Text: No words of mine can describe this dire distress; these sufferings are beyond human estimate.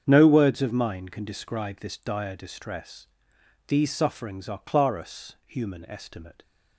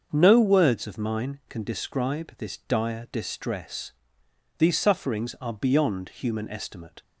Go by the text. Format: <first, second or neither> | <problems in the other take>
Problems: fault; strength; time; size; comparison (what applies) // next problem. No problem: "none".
second | starts louder than the rest; strong; until 1.0 s; 7.5 dB; also in the second // says "clarus" for "beyond"; at 4.5 s